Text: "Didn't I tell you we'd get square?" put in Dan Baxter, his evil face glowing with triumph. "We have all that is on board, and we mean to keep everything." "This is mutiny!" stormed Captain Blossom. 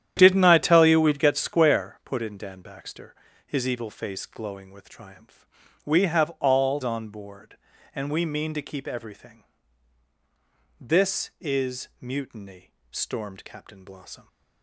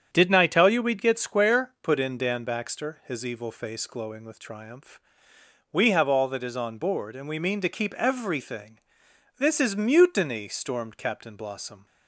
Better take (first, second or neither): second